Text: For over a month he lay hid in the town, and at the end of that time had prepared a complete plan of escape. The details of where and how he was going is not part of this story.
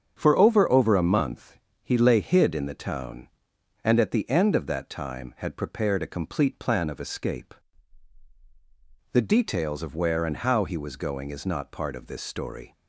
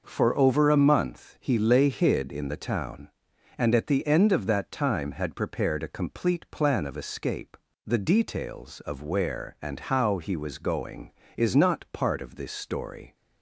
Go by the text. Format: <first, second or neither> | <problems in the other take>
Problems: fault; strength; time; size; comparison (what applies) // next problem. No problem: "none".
second | starts louder than the rest; strong; until 1.2 s; 7.5 dB // says "over" twice; at 0.7 s // pauses between "month" and "he"; slight; at 1.5 s; 0.26 s long